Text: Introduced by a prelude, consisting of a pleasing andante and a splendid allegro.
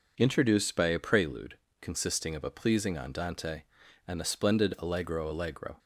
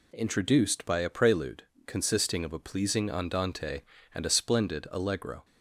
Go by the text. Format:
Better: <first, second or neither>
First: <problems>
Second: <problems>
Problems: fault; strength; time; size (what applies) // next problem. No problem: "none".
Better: second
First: says "allegro" twice; at 5.3 s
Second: none